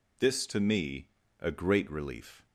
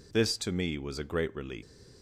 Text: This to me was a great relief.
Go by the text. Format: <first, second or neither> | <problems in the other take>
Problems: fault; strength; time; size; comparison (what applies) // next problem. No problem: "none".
second | skips "was"; at 1.2 s